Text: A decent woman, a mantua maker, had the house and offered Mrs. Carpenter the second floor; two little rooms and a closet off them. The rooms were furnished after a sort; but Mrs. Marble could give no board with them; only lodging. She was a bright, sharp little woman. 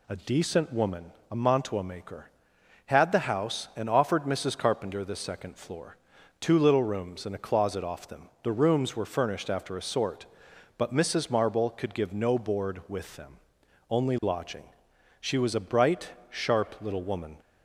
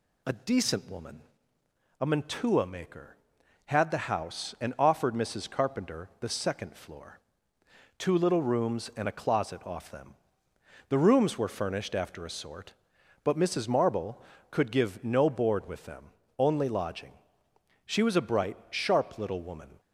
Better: neither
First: none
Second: none

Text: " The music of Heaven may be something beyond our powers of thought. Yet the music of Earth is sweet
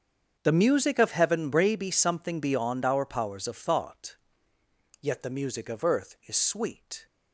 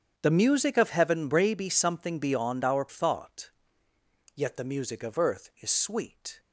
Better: first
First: starts louder than the rest; until 1.4 s; 7 dB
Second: starts louder than the rest; strong; until 1.1 s; 8 dB // skips "powers of"; at 2.8 s

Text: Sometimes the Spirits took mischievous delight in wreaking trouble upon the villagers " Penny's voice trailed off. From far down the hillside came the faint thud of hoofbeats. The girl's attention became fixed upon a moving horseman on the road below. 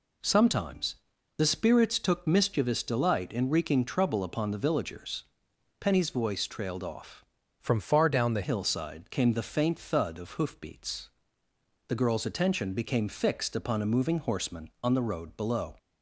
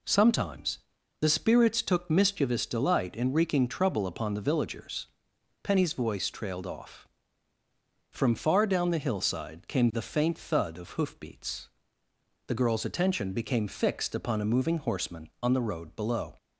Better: second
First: pauses between "Sometimes" and "the"; at 0.9 s; 0.42 s long // changes voice from "From" to "the"; from 7.5 to 8.4 s; 0.9 s long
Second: pauses between "Sometimes" and "the"; at 0.7 s; 0.42 s long

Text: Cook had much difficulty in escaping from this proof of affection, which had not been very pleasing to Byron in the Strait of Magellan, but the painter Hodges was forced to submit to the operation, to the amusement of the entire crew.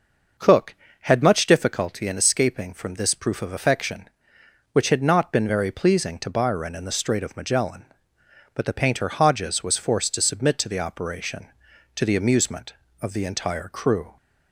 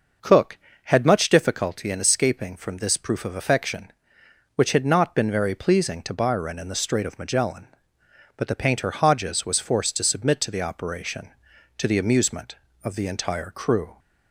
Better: neither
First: none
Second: none

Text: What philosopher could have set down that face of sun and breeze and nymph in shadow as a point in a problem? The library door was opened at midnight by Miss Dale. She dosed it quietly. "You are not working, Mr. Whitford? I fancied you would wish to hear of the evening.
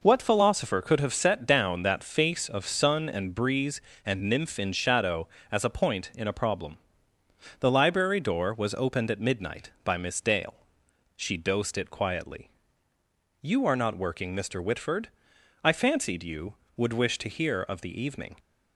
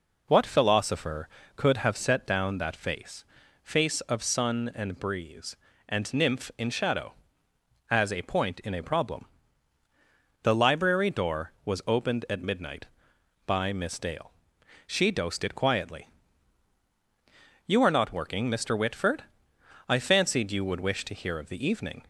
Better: first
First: none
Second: says "face" twice; at 3.6 s

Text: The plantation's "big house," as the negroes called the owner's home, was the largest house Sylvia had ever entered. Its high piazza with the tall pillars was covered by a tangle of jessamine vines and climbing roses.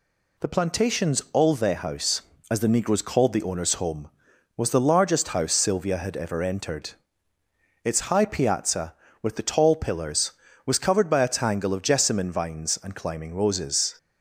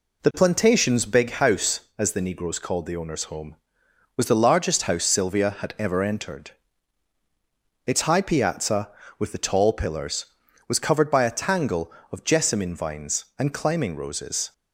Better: second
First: says "olve" for "big"; at 1.3 s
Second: none

